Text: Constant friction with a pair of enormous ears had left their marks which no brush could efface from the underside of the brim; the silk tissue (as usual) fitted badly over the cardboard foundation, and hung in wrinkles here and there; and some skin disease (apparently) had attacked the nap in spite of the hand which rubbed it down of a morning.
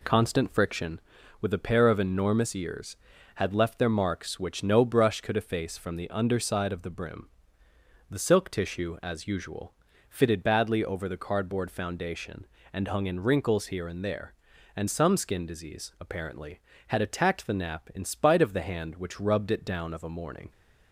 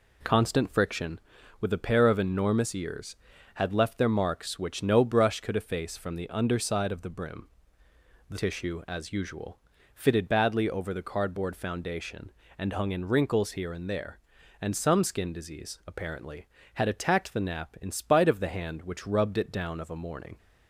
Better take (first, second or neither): first